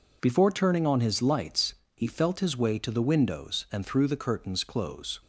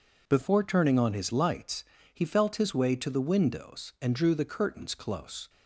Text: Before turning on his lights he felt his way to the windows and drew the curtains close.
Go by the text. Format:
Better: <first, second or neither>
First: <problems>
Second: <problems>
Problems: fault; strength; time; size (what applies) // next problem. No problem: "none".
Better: second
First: pauses between "lights" and "he"; slight; at 1.7 s; 0.22 s long // says "threw" for "drew"; at 3.8 s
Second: pauses between "lights" and "he"; slight; at 1.8 s; 0.28 s long